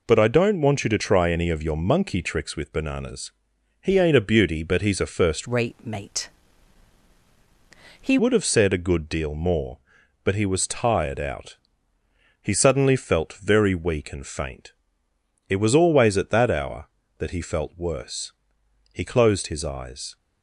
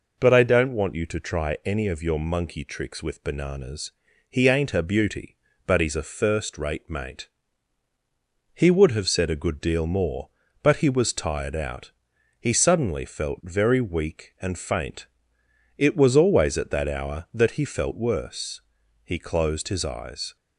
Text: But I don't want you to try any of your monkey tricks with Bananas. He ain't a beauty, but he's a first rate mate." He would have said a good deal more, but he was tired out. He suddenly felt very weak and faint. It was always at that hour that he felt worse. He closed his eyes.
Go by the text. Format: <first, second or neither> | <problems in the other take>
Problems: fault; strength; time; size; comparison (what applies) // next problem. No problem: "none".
second | changes voice from "rate" to "He"; from 5.4 to 8.1 s; 2.7 s long